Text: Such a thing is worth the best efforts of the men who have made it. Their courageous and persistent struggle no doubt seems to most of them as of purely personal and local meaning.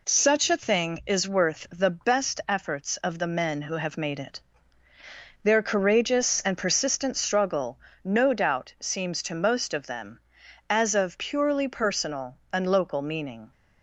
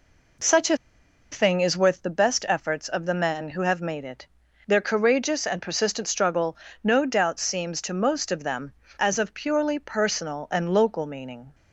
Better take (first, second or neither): first